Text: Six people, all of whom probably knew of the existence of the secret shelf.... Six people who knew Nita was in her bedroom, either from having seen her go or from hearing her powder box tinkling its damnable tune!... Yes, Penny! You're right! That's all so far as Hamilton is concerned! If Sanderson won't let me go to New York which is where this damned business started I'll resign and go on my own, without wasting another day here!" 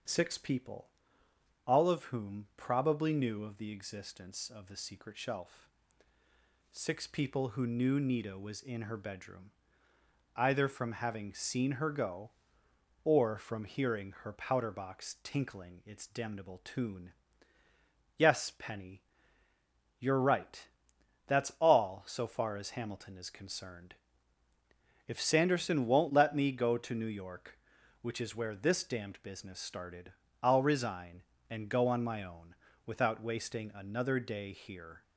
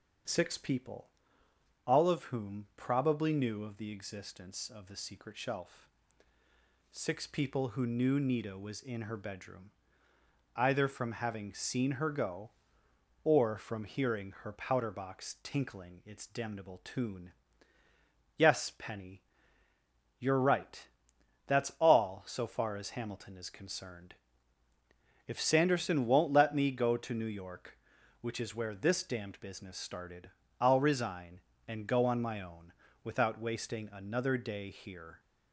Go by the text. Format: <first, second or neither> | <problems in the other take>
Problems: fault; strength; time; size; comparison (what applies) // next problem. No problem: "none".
neither | starts louder than the rest; the same in both // pauses between "started" and "I'll"; slight; the same in both